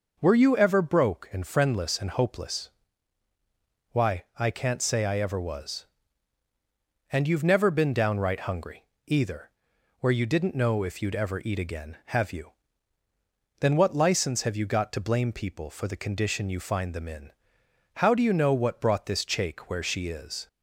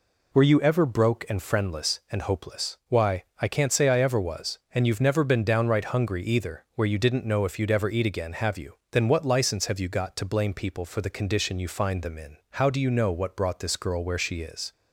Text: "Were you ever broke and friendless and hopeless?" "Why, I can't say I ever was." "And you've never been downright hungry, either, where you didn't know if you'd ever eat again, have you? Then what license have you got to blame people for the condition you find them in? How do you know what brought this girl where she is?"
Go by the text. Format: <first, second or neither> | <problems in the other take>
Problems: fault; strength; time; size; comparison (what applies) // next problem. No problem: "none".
second | says "chake" for "girl"; at 19.2 s